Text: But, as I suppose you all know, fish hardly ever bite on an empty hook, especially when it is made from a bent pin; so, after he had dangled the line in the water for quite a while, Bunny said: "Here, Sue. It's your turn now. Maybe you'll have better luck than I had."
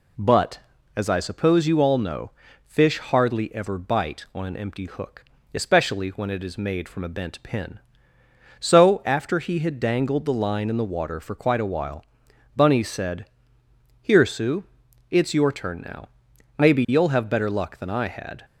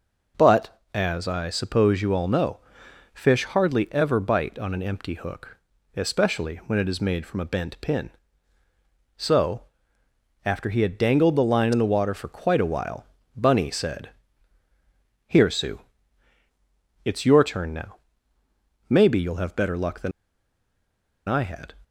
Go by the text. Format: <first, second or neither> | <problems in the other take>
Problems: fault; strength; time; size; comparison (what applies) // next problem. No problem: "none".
first | pauses between "than" and "I"; at 20.1 s; 1.1 s long